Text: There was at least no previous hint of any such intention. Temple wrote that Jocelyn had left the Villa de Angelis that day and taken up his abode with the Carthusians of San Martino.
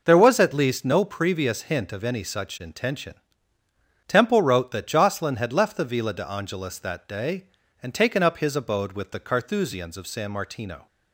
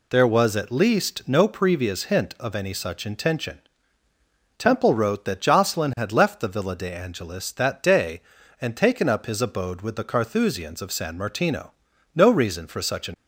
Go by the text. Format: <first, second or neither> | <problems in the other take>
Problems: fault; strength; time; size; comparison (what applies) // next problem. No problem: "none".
first | goes on to say "No reason for such an"; noticeable; from 12.1 s on; 1.0 s long